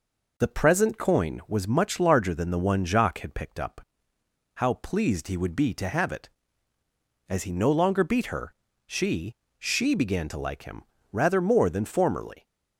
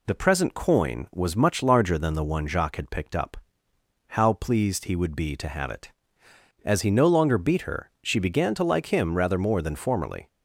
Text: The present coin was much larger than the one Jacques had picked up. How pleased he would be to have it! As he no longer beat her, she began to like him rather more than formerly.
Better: second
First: says "she" twice; at 9.5 s // pauses between "him" and "rather"; slight; at 10.8 s; 0.28 s long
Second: none

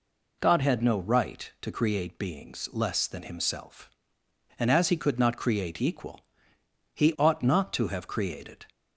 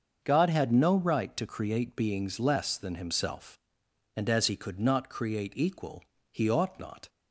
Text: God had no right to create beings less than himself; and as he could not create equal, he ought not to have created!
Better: first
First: none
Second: starts louder than the rest; until 1.2 s; 6.5 dB // stops before "to have created"; at 7.0 s

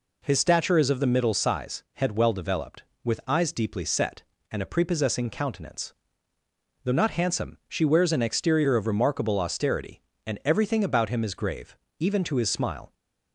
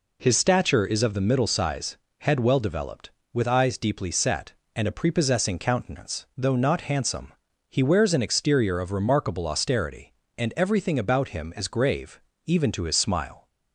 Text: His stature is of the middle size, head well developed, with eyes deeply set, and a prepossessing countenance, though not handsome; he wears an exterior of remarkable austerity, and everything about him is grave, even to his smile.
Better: second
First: says "she" for "he"; at 7.6 s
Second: none

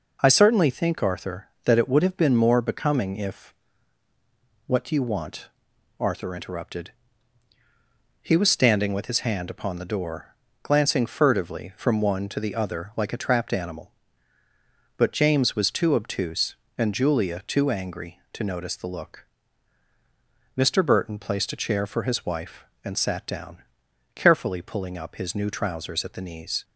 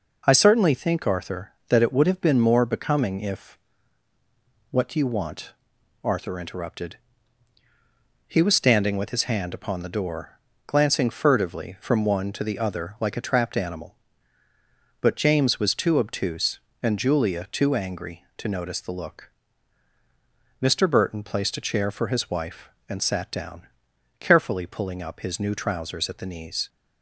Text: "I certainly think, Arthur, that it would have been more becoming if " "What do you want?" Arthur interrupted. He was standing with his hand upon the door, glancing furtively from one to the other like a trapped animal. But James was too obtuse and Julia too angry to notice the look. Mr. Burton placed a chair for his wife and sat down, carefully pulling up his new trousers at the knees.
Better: neither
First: none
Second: none

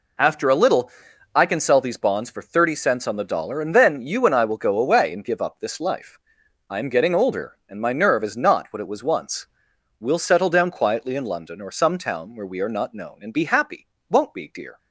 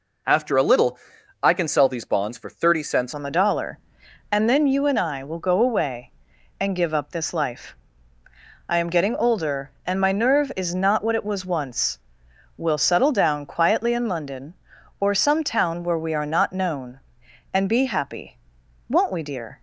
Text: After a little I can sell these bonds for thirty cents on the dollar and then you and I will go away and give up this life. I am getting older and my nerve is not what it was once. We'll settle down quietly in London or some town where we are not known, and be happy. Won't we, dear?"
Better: first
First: pauses between "little" and "I"; at 0.9 s; 0.44 s long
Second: pauses between "little" and "I"; at 0.9 s; 0.44 s long // changes voice at "on"; from 3.1 s on; 16.5 s long

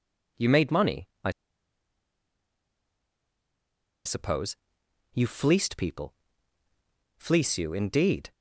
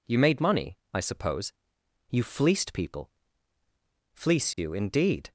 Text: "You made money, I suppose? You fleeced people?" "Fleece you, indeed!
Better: second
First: pauses between "I" and "suppose"; strong; at 1.3 s; 2.7 s long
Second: none

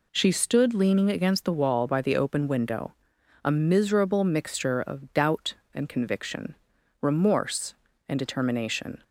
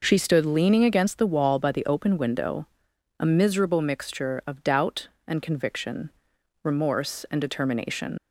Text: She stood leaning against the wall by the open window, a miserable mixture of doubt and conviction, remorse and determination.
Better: first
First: none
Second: leaves "determination" unfinished; at 8.1 s; 95 ms

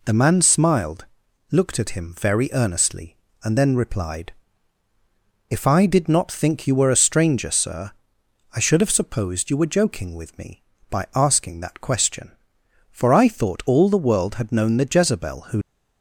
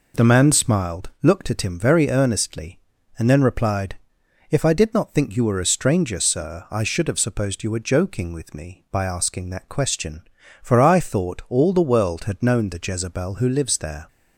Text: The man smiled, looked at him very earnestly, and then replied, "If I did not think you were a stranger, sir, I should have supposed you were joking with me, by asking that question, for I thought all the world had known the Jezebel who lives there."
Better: second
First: stops before "lives there"; at 15.6 s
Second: none

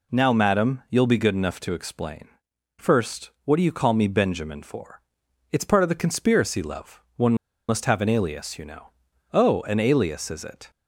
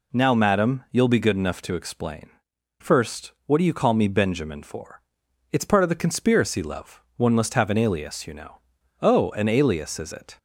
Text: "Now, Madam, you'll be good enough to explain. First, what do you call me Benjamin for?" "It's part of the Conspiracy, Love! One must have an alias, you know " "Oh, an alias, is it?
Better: second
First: pauses between "One" and "must"; slight; at 7.3 s; 0.34 s long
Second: none

